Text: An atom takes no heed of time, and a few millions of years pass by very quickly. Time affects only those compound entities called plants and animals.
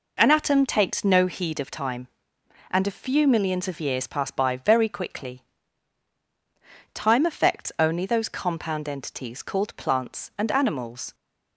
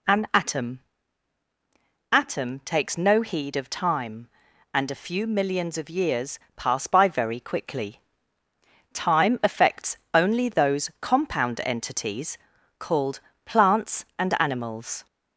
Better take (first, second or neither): first